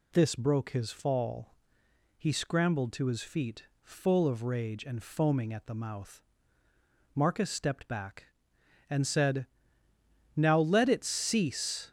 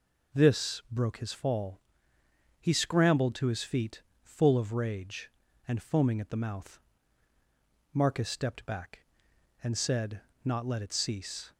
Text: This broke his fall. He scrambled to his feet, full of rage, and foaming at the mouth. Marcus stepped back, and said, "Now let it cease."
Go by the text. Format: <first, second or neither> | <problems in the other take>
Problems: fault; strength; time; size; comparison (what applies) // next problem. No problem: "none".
first | says "Not" for "Now"; at 10.4 s